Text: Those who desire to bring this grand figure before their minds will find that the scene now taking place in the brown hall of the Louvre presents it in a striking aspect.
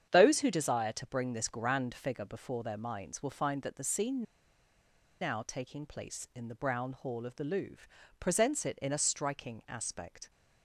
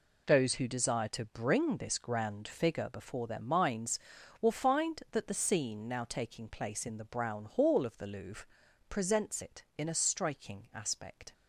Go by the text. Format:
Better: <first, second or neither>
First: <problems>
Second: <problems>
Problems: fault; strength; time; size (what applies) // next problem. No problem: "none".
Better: second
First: starts louder than the rest; strong; until 1.1 s; 8.5 dB // pauses between "scene" and "now"; at 4.2 s; 0.98 s long // pauses between "Louvre" and "presents"; slight; at 7.8 s; 0.34 s long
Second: pauses between "Louvre" and "presents"; at 8.4 s; 0.42 s long